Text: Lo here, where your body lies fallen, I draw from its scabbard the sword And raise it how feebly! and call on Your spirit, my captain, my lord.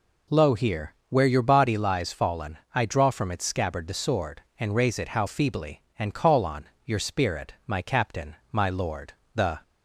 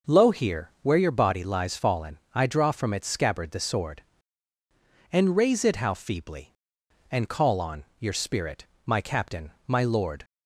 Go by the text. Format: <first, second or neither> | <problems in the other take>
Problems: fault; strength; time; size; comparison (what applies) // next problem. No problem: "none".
second | pauses between "on" and "Your"; slight; at 6.6 s; 0.18 s long; slight in the second // goes on to say "The"; slight; from 9.3 s on; 0.26 s long